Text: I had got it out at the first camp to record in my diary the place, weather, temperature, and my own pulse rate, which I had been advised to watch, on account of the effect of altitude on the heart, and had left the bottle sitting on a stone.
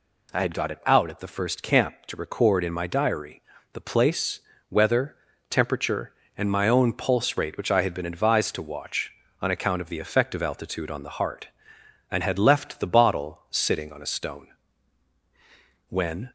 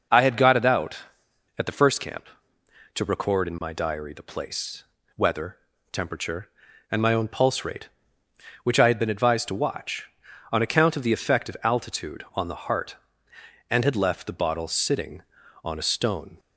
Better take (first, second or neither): second